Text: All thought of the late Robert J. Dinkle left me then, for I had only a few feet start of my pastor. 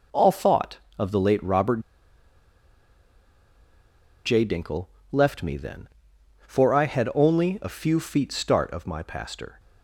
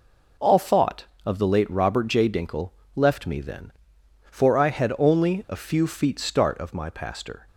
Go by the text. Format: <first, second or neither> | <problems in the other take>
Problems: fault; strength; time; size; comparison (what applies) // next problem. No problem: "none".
second | pauses between "Robert" and "J"; strong; at 1.8 s; 2.4 s long // pauses between "Dinkle" and "left"; slight; at 4.8 s; 0.24 s long; slight in the second